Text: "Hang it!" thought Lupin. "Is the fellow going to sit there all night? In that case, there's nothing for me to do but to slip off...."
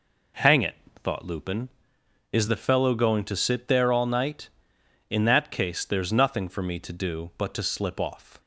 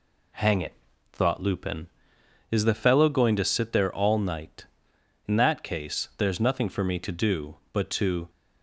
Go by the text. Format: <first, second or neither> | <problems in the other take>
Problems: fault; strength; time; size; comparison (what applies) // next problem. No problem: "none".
first | stops before "slip off"; at 8.2 s